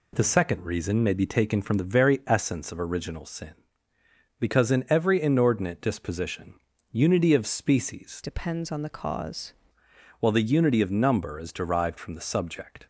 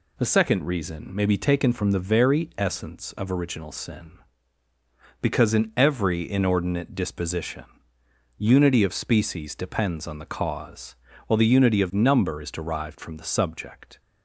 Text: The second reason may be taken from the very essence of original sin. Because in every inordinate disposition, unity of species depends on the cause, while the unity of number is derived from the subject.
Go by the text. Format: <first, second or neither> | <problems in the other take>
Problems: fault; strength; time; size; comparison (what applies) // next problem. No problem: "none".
second | changes voice from "depends" to "cause"; from 8.2 to 9.5 s; 1.3 s long